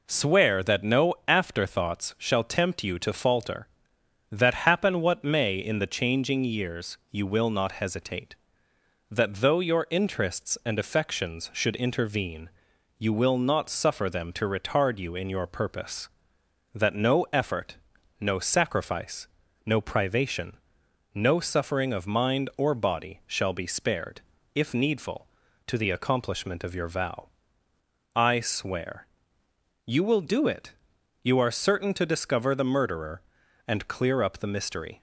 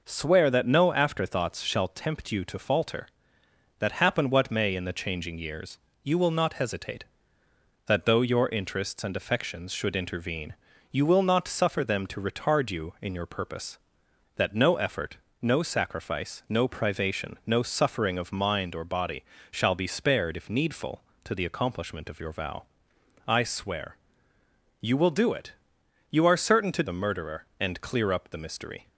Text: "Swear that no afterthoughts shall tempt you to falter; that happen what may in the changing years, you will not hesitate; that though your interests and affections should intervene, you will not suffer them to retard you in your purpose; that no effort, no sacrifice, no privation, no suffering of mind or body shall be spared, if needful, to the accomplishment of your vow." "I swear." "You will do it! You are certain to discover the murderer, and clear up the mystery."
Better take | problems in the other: first | pauses between "body" and "shall"; slight; at 19.2 s; 0.28 s long // skips "discover"; at 26.8 s

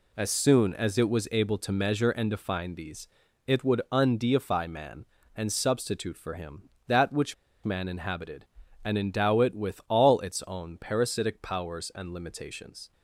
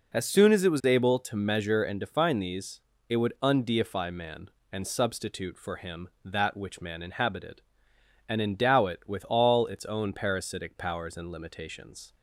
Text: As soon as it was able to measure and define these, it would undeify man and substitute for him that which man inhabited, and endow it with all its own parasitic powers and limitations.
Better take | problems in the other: second | pauses between "which" and "man"; slight; at 7.3 s; 0.31 s long

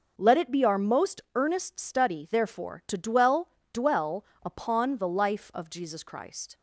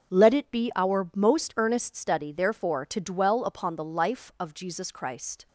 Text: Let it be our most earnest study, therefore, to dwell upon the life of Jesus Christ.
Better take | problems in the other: second | starts louder than the rest; noticeable; until 1.1 s; 6 dB; strong in the second // says "dwell" twice; at 3.7 s

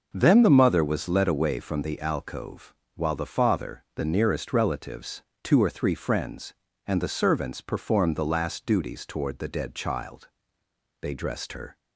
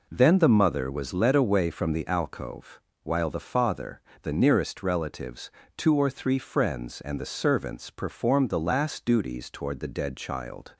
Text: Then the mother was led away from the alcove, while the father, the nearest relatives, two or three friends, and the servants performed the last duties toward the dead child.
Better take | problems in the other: second | goes on to say "They dressed her"; noticeable; from 11.0 s on; 0.76 s long

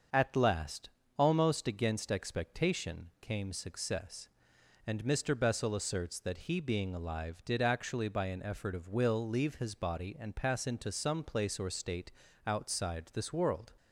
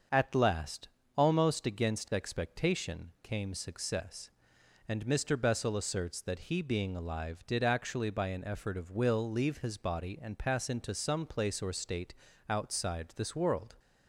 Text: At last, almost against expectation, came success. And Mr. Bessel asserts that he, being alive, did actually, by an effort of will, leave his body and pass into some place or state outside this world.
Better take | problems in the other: neither | starts louder than the rest; the same in both // pauses between "state" and "outside"; slight; the same in both

